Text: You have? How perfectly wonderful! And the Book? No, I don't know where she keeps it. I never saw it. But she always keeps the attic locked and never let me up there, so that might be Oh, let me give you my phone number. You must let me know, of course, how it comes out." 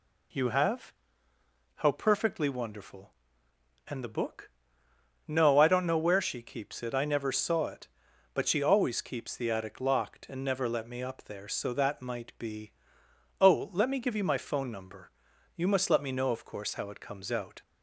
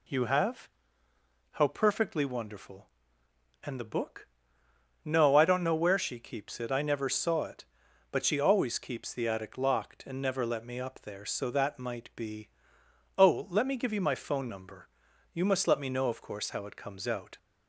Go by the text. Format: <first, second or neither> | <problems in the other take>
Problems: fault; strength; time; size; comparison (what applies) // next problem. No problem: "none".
neither | pauses between "be" and "Oh"; noticeable; the same in both